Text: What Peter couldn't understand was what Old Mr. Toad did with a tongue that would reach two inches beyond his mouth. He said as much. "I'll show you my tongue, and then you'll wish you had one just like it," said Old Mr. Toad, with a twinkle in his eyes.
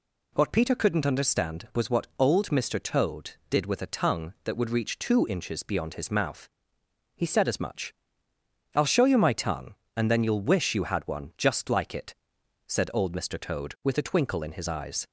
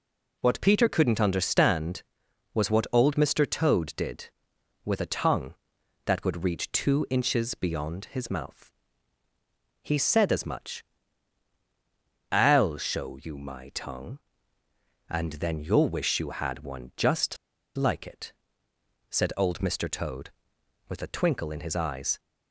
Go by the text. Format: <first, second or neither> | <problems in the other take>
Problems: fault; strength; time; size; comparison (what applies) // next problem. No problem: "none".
first | pauses between "just" and "like"; at 17.3 s; 0.39 s long